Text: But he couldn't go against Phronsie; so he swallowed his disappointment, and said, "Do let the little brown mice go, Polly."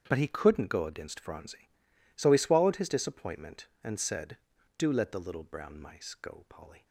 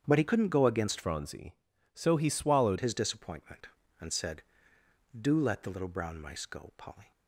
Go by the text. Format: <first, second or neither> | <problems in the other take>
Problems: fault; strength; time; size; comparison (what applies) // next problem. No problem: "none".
first | starts louder than the rest; strong; until 1.0 s; 8 dB; strong in the first // changes voice from "Phronsie" to "swallowed"; from 1.0 to 2.7 s; 1.7 s long